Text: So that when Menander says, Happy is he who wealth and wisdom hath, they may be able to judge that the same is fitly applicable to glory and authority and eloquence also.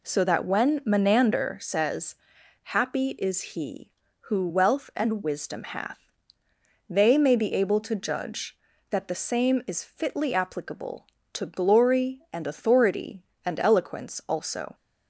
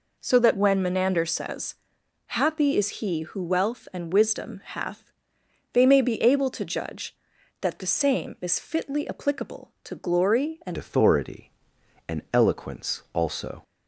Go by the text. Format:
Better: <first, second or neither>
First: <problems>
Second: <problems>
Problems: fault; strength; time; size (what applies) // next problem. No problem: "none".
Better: first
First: none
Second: changes voice at "authority"; from 10.7 s on; 2.9 s long